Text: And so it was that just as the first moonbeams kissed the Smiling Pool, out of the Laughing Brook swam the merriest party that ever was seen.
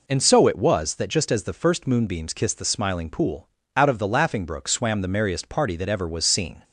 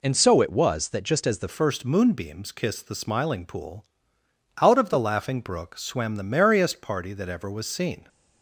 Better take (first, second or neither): first